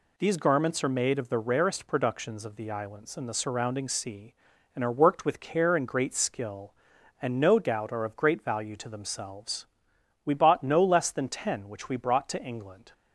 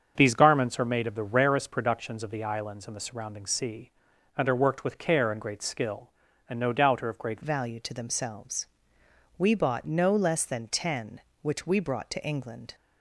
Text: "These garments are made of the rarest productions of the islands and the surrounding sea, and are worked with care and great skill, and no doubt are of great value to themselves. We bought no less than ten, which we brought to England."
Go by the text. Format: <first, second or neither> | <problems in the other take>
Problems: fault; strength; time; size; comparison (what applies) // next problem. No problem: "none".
first | starts louder than the rest; until 1.1 s; 7 dB // changes voice at "value"; from 7.4 s on; 5.3 s long